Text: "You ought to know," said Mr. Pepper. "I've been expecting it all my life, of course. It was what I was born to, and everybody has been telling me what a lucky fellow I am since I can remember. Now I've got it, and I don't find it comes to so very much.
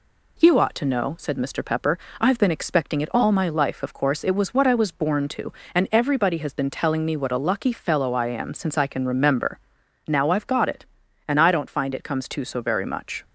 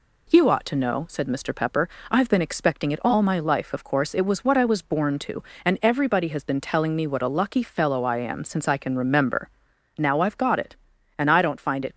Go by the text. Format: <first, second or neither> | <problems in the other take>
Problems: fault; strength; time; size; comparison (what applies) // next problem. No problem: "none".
first | stops before "comes to so very much"; at 11.9 s